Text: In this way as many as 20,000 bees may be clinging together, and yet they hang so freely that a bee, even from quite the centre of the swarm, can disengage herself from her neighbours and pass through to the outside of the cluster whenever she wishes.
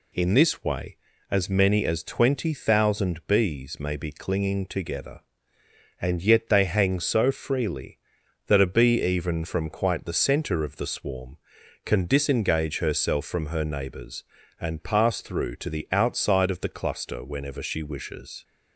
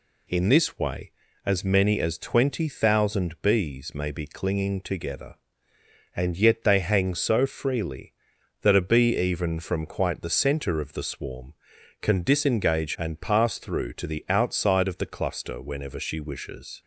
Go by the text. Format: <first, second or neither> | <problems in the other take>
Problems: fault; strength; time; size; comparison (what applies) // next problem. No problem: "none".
first | skips "herself from her neighbours"; at 12.9 s